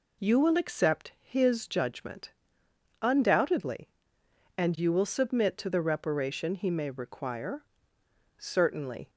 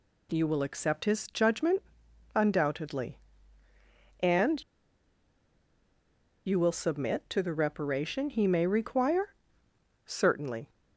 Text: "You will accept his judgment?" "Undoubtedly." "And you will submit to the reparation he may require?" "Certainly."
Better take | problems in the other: first | pauses between "And" and "you"; strong; at 4.6 s; 1.8 s long

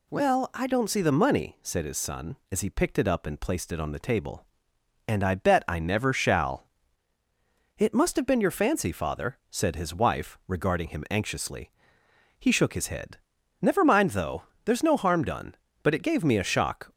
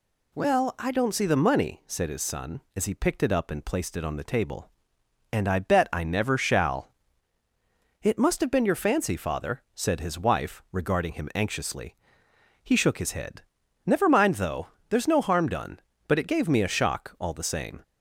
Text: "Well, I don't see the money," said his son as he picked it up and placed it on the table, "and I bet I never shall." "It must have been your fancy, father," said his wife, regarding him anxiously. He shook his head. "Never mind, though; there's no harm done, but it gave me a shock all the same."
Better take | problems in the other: second | stops before "all the same"; at 16.9 s

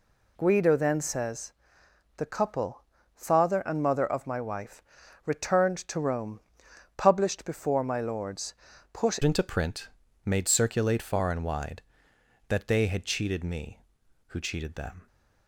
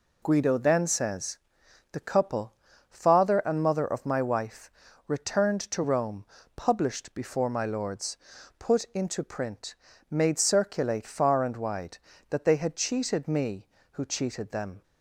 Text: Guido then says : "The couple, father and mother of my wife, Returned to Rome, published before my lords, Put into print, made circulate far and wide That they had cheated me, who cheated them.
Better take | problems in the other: second | changes voice at "into"; from 9.2 s on; 5.8 s long

